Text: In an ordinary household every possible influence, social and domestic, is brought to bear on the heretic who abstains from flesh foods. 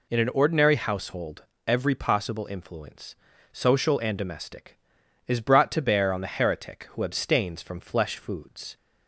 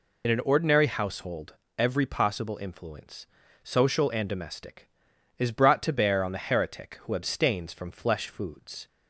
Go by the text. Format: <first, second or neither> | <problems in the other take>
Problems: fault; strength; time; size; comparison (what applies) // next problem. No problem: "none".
first | loses the start of "In"; at 0.2 s; 45 ms // pauses between "household" and "every"; slight; at 1.5 s; 0.22 s long; slight in the first